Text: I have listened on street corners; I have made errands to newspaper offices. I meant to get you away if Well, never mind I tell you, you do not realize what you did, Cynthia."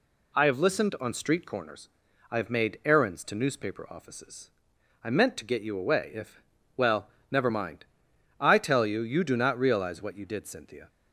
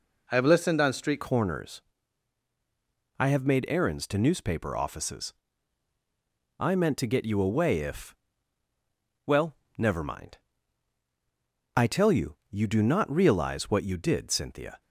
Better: first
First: pauses between "if" and "Well"; slight; at 6.4 s; 0.34 s long // pauses between "mind" and "I"; noticeable; at 7.8 s; 0.56 s long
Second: changes voice at "corners"; from 1.2 s on; 13.6 s long // pauses between "if" and "Well"; at 8.1 s; 1.1 s long // pauses between "mind" and "I"; strong; at 10.3 s; 1.3 s long

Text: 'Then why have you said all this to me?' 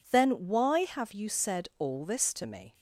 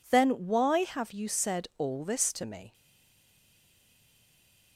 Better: first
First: none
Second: stays silent after the last word; noticeable; from 2.7 s on; 2.0 s long

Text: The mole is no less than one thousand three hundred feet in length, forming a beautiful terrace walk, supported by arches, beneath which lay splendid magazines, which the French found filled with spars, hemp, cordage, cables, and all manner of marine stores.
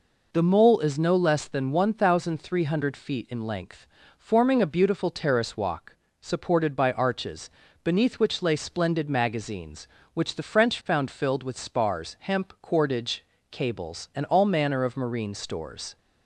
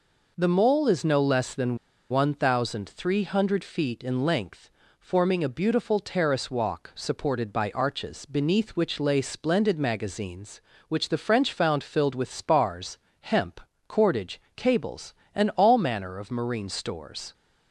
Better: first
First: none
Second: pauses between "than" and "one"; slight; at 1.7 s; 0.34 s long

